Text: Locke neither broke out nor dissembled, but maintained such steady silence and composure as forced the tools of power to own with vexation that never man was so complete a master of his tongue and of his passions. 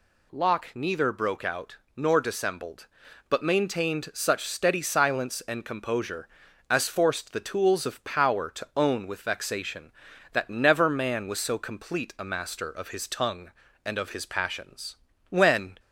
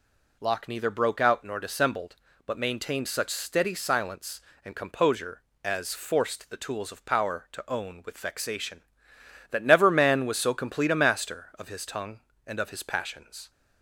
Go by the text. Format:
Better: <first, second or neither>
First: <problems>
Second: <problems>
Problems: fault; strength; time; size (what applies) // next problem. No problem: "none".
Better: second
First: pauses between "out" and "nor"; slight; at 1.7 s; 0.18 s long // goes on to say "When"; from 15.2 s on; 0.50 s long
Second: none